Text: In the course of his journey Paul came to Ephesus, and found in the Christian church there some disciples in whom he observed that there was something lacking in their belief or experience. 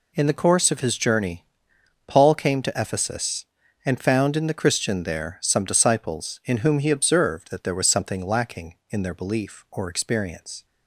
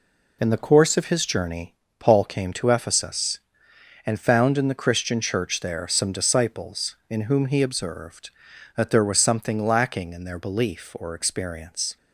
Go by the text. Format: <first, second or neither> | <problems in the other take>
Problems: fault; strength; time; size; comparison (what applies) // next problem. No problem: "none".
second | pauses between "journey" and "Paul"; noticeable; at 1.4 s; 0.64 s long; slight in the second // skips "church"; at 5.0 s